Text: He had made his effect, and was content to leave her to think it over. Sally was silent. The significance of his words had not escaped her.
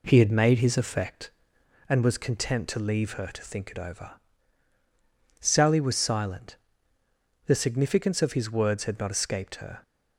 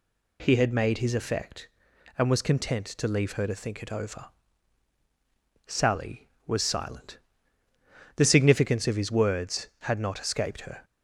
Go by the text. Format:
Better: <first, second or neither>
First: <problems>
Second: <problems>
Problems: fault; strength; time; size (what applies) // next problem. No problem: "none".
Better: second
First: starts louder than the rest; slight; until 1.8 s; 3 dB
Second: none